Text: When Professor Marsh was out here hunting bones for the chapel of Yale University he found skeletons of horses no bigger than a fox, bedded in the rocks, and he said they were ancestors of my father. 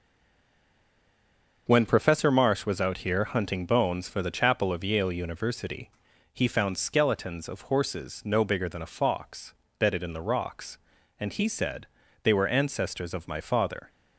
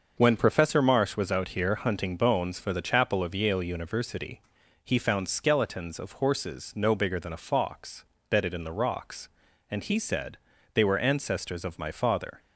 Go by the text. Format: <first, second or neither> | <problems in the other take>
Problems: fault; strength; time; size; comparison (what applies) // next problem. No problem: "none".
second | stays silent before the first word; noticeable; until 1.6 s; 1.6 s long // starts louder than the rest; until 2.6 s; 6 dB; also in the second // pauses between "University" and "he"; at 5.8 s; 0.42 s long; also in the second // pauses between "said" and "they"; slight; at 11.8 s; 0.34 s long; slight in the second